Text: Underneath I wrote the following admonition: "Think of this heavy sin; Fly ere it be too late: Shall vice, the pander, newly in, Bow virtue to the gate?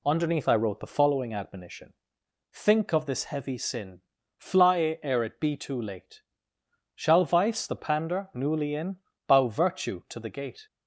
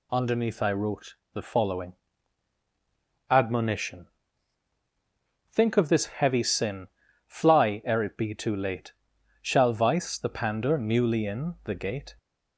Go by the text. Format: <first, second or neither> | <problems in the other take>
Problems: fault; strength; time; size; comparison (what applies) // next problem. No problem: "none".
first | pauses between "wrote" and "the"; slight; at 1.1 s; 0.18 s long // pauses between "following" and "admonition"; strong; at 1.9 s; 1.3 s long // skips "Bow virtue to"; at 11.5 s